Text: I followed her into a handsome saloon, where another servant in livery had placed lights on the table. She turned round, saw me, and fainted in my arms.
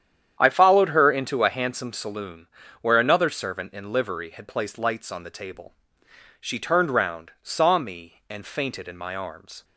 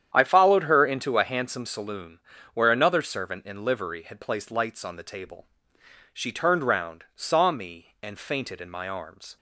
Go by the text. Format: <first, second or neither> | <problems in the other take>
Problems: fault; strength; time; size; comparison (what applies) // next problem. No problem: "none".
neither | starts louder than the rest; strong; the same in both